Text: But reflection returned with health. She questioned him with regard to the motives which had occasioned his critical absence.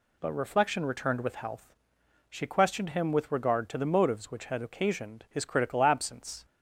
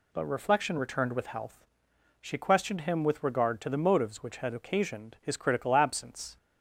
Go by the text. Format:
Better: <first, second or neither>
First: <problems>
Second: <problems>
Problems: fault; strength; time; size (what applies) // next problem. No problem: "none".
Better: neither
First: none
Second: none